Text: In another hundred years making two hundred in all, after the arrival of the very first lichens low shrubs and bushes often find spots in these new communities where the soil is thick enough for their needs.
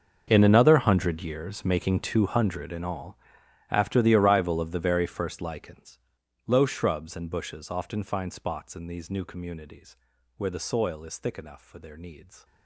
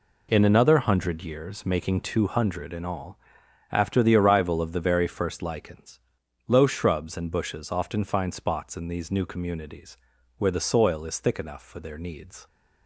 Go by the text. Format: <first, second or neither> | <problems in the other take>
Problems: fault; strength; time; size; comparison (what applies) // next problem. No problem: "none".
second | gets quieter; strong; throughout; 18.5 dB // pauses between "lichens" and "low"; noticeable; at 5.9 s; 0.46 s long; noticeable in the second // pauses between "communities" and "where"; at 9.9 s; 0.40 s long; also in the second